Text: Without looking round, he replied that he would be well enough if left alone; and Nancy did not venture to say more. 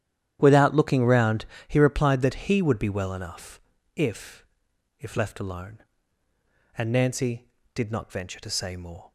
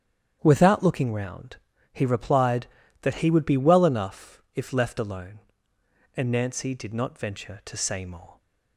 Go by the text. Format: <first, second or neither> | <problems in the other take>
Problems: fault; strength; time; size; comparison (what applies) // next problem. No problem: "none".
second | starts louder than the rest; strong; until 1.4 s; 10.5 dB; strong in the second // pauses between "enough" and "if"; slight; at 3.6 s; 0.34 s long // says "if" twice; at 4.9 s